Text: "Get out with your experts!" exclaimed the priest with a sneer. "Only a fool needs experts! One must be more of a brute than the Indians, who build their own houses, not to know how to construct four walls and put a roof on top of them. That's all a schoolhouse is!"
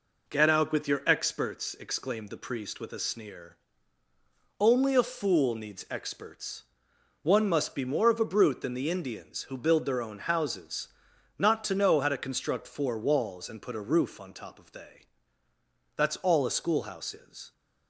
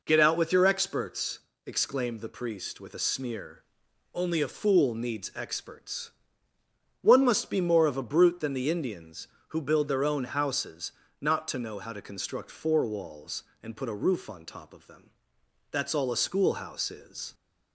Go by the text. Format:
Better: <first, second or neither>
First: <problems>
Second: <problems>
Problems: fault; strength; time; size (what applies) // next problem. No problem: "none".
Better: second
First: says "they" for "them"; at 14.7 s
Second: none